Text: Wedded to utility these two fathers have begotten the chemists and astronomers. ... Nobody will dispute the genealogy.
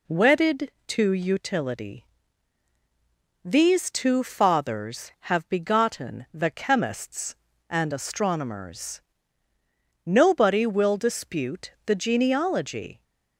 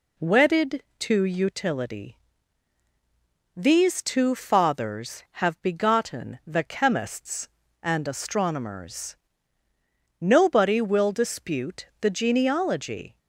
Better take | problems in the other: neither | pauses between "utility" and "these"; strong; the same in both

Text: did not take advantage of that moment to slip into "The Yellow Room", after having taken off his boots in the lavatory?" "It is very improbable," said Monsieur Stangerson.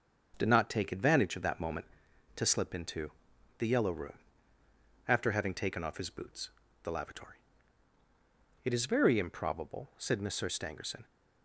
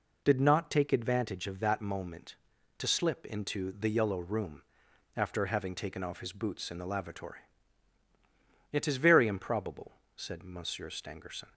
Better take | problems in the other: second | starts louder than the rest; until 1.3 s; 6.5 dB // pauses between "into" and "The"; noticeable; at 3.1 s; 0.48 s long // skips "in"; at 6.6 s

